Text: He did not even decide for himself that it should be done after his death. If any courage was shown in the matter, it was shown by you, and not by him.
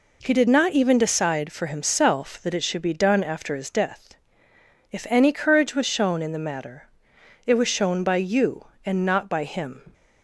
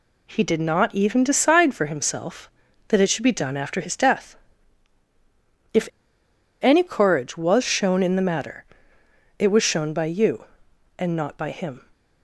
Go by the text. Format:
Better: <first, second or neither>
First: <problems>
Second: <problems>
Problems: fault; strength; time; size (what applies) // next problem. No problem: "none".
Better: first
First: none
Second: pauses between "If" and "any"; noticeable; at 5.8 s; 0.74 s long